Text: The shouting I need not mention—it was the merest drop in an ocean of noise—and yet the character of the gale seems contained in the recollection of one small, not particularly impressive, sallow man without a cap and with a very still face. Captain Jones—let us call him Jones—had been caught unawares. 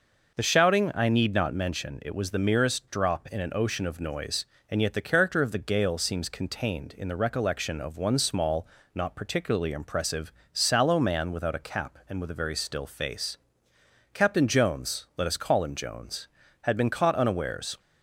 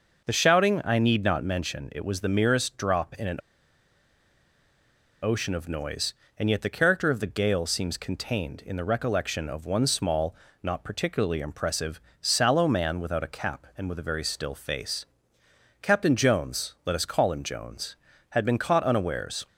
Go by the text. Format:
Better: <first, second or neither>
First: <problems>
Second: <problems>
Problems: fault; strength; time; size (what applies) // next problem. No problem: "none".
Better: first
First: none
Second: pauses between "an" and "ocean"; strong; at 3.3 s; 1.8 s long